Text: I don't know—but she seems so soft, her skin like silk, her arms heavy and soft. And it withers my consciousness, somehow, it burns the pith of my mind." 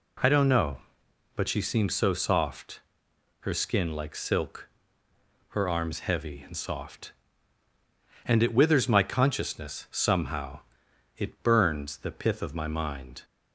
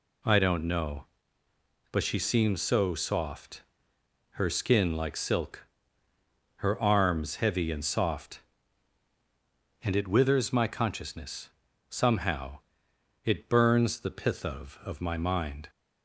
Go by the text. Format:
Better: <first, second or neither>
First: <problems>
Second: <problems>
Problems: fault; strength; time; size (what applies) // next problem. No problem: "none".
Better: first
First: none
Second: says "of" twice; at 14.8 s